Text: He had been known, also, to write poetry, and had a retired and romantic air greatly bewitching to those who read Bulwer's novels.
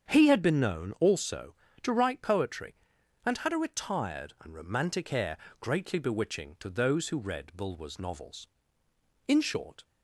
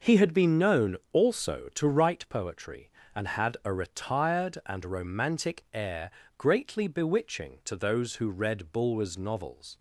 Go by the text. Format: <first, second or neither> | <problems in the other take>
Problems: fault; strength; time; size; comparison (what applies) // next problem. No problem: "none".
second | starts louder than the rest; strong; until 1.1 s; 7.5 dB // pauses between "air" and "greatly"; slight; at 5.3 s; 0.24 s long; slight in the second // goes on to say "In short"; from 9.2 s on; 0.58 s long